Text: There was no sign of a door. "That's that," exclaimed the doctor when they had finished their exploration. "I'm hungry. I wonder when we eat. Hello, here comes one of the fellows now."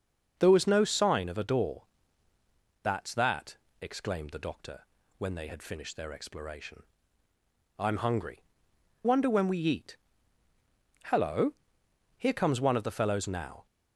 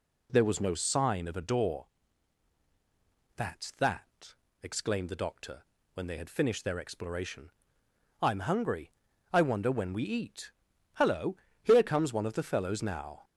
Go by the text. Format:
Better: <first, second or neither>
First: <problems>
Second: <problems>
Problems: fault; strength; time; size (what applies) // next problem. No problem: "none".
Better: second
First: pauses between "doctor" and "when"; slight; at 4.8 s; 0.34 s long // skips "I"; at 8.7 s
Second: pauses between "doctor" and "when"; slight; at 5.6 s; 0.30 s long